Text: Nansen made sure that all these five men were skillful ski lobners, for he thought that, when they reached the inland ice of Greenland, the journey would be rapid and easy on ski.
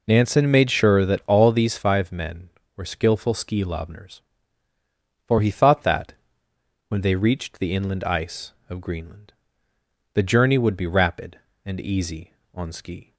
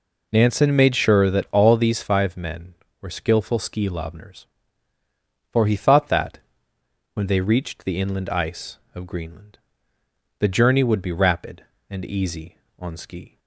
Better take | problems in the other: neither | none

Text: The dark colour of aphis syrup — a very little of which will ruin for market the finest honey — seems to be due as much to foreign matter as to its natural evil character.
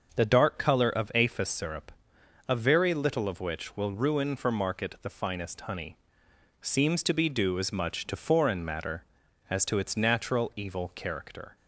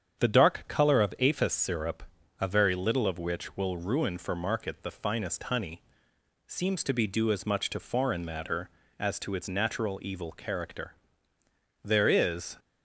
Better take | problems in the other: first | starts louder than the rest; strong; until 1.3 s; 8 dB; also in the first // goes on to say "There is"; noticeable; from 11.8 s on; 0.74 s long

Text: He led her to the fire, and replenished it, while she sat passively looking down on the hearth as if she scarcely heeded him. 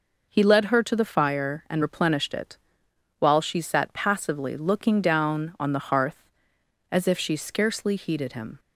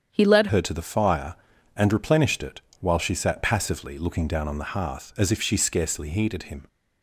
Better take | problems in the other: first | starts louder than the rest; strong; until 1.1 s; 8 dB // changes voice at "her"; from 0.4 s on; 6.2 s long

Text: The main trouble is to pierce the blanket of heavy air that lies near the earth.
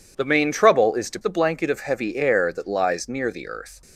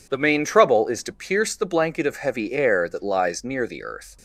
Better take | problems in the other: second | skips "pierce"; at 1.1 s

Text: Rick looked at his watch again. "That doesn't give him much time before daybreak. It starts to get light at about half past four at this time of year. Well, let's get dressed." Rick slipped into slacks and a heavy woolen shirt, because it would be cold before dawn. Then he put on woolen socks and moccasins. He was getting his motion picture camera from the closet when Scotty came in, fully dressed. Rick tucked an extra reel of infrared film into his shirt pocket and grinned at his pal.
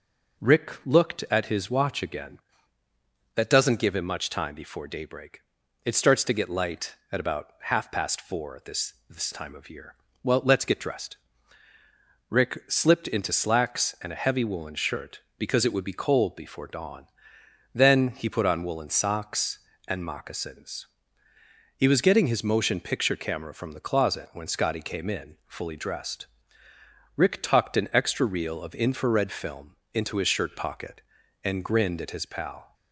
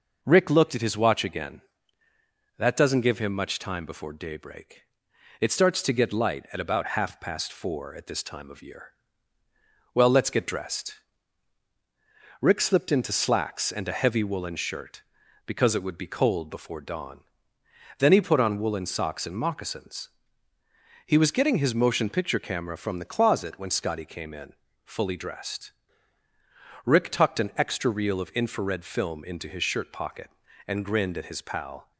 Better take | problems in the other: second | says "this" twice; at 9.0 s // pauses between "film" and "into"; slight; at 29.7 s; 0.18 s long

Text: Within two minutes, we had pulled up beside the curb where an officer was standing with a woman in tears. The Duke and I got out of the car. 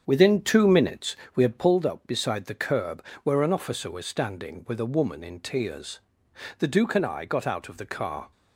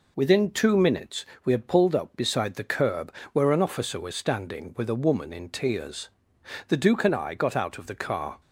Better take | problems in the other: second | starts louder than the rest; strong; until 1.7 s; 7.5 dB // pauses between "curb" and "where"; slight; at 3.0 s; 0.18 s long; slight in the second

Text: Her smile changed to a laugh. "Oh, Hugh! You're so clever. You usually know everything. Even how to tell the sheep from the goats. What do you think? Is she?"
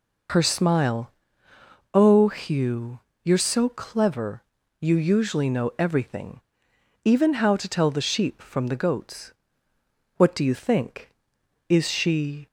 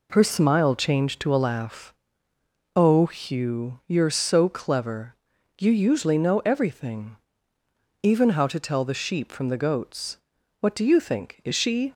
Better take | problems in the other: second | skips "changed to a laugh"; at 1.5 s

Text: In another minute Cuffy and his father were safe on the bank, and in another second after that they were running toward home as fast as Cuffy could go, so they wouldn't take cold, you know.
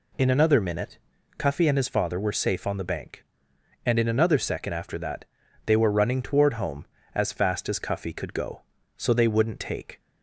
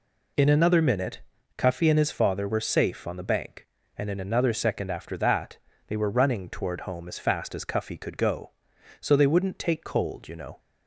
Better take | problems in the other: second | pauses between "minute" and "Cuffy"; at 0.9 s; 0.40 s long; slight in the second // pauses between "that" and "they"; at 5.2 s; 0.40 s long; slight in the second // stops before "cold you know"; at 9.9 s

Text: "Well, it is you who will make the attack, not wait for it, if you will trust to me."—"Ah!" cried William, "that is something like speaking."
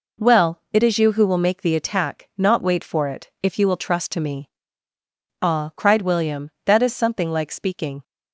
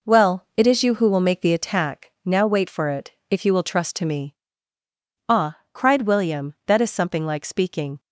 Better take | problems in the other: first | says "now" for "not"; at 2.2 s

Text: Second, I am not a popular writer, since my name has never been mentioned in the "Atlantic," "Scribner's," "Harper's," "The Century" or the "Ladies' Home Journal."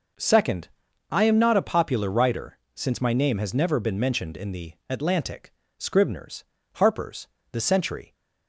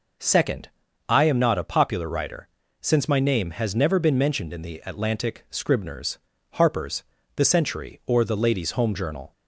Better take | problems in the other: second | stops before "or the Ladies Home Journal"; at 8.1 s

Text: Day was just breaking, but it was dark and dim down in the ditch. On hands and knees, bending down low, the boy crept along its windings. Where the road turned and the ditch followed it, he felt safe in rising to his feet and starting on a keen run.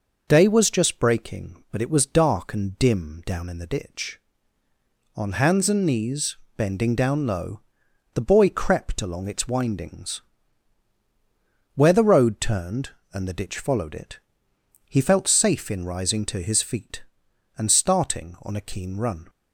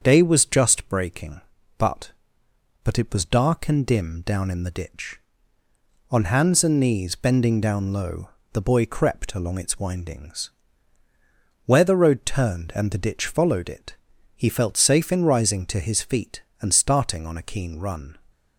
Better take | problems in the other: first | starts louder than the rest; until 1.0 s; 7 dB // says "but" twice; at 2.8 s

